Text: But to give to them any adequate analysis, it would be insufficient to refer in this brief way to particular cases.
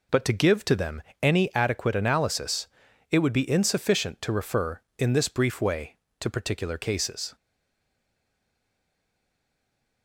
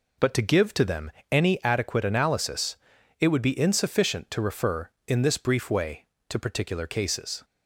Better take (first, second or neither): second